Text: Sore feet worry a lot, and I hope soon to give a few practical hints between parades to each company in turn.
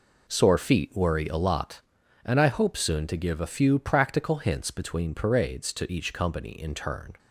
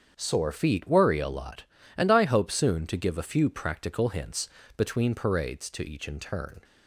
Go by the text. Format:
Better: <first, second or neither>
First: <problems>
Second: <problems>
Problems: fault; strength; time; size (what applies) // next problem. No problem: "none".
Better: first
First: none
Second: starts louder than the rest; strong; until 1.1 s; 7.5 dB // pauses between "hints" and "between"; slight; at 4.4 s; 0.28 s long // skips "company"; at 6.0 s